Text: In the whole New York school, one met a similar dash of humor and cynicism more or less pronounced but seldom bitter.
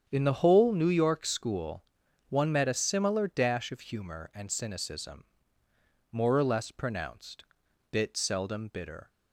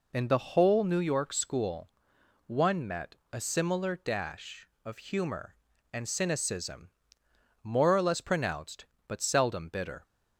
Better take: second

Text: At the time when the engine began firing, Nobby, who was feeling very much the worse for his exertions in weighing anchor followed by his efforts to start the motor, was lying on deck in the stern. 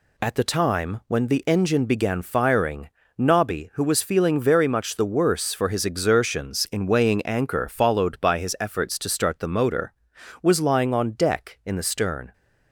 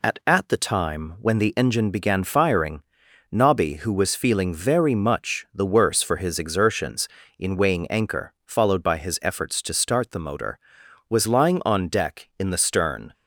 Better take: first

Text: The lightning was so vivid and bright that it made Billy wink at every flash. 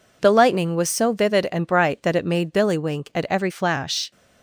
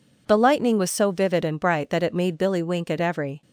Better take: first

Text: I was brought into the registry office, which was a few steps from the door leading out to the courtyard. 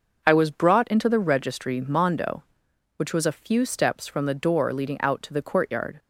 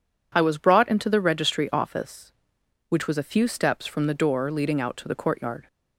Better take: second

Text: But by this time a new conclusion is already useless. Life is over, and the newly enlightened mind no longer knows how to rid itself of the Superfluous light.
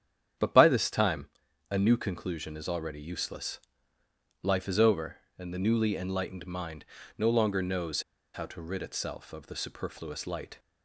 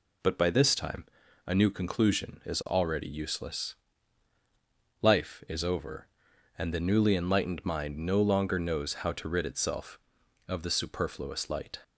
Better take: second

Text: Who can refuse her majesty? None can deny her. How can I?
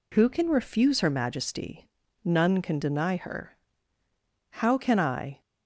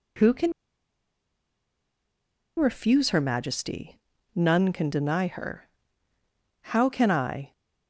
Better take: first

